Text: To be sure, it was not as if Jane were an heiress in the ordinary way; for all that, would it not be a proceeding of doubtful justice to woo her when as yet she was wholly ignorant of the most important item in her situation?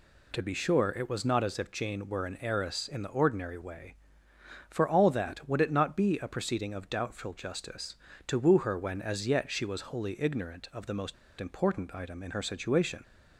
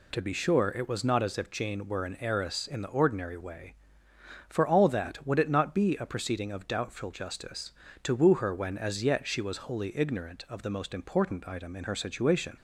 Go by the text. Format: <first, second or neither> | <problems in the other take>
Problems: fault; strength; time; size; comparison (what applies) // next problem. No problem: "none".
second | pauses between "most" and "important"; slight; at 11.1 s; 0.25 s long